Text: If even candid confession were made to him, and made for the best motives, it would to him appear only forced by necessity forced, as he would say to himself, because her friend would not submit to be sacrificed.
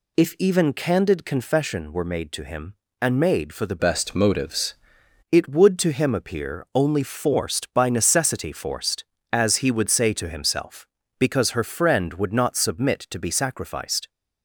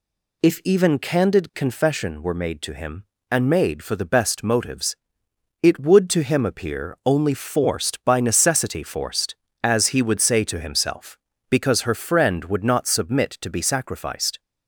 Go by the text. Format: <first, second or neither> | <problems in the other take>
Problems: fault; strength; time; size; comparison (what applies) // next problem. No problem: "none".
second | changes voice from "best" to "motives"; from 3.7 to 4.7 s; 1.0 s long